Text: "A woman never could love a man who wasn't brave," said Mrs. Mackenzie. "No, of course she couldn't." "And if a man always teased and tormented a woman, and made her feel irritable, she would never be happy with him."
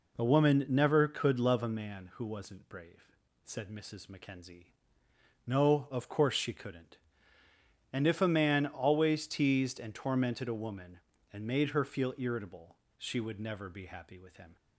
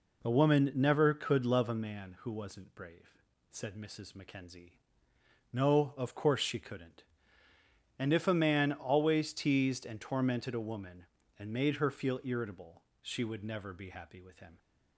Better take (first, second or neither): neither